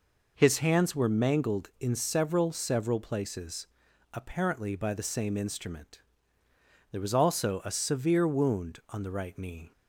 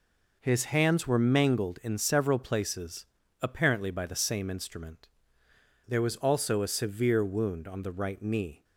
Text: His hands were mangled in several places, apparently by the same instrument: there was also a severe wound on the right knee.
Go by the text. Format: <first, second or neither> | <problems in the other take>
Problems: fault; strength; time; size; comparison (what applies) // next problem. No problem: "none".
second | says "several" twice; at 2.5 s